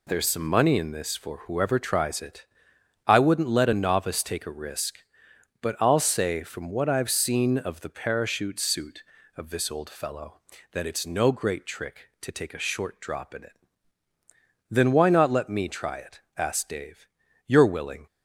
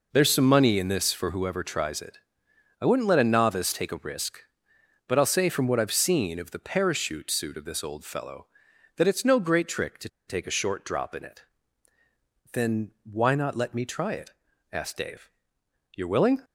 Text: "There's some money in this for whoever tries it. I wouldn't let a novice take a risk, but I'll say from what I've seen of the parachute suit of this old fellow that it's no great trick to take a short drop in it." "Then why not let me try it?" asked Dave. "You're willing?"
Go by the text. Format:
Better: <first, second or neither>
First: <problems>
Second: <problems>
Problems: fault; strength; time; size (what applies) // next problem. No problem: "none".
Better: first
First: none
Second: pauses between "to" and "take"; slight; at 10.0 s; 0.19 s long